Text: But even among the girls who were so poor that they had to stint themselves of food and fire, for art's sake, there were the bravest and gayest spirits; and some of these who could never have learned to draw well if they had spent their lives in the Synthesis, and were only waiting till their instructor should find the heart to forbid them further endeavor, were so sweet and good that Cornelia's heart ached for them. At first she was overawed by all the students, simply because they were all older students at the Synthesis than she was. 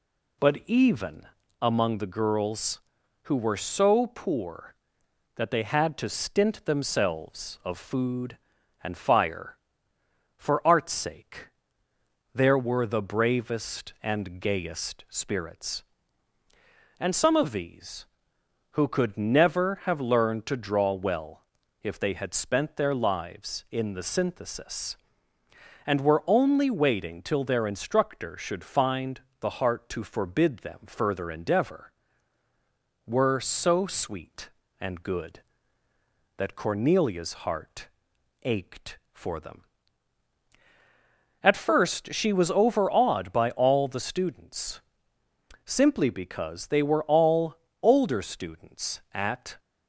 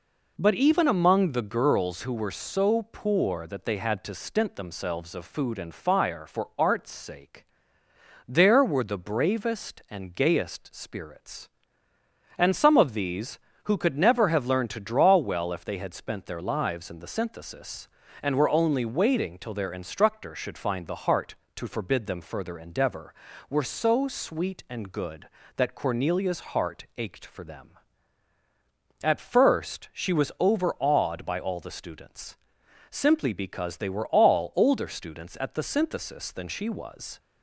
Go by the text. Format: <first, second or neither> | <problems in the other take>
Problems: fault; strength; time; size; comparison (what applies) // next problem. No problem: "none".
second | pauses between "even" and "among"; at 1.2 s; 0.38 s long // pauses between "well" and "if"; at 21.4 s; 0.40 s long // pauses between "find" and "the"; slight; at 29.1 s; 0.20 s long // pauses between "heart" and "ached"; noticeable; at 37.8 s; 0.54 s long // pauses between "all" and "older"; slight; at 47.5 s; 0.26 s long // stops before "the Synthesis than she was"; at 49.5 s